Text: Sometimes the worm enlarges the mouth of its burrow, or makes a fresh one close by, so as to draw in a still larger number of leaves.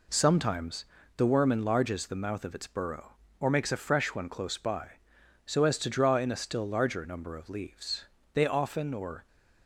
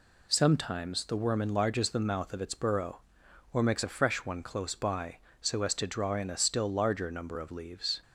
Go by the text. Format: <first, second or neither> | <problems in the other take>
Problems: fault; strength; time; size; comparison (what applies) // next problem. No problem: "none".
second | pauses between "Sometimes" and "the"; slight; at 0.8 s; 0.32 s long // goes on to say "They often or"; noticeable; from 8.3 s on; 0.94 s long